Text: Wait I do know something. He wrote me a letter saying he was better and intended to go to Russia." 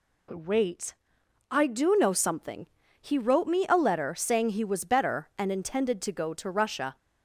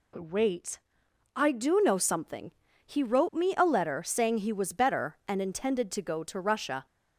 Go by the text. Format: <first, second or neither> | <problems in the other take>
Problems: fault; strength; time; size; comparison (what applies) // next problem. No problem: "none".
neither | pauses between "Wait" and "I"; noticeable; the same in both